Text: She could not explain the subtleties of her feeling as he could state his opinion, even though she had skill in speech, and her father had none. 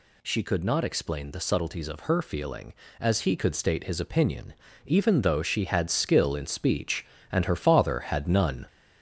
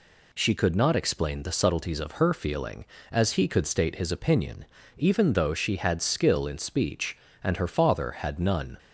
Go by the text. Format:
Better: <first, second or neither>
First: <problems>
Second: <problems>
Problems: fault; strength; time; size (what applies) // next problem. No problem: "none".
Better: second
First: gets louder; noticeable; throughout; 4.5 dB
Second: none